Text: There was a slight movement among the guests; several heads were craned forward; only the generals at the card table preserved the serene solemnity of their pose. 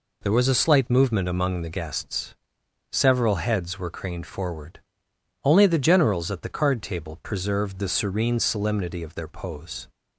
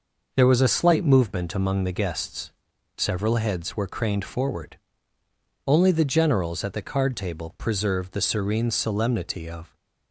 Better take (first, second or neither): first